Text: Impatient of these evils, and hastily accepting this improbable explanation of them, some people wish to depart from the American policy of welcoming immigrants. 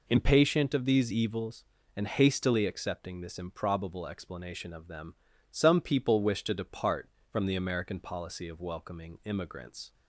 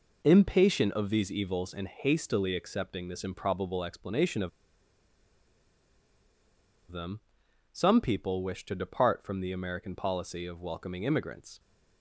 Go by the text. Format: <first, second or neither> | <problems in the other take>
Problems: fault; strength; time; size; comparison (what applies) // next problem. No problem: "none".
first | pauses between "of" and "them"; strong; at 4.4 s; 2.4 s long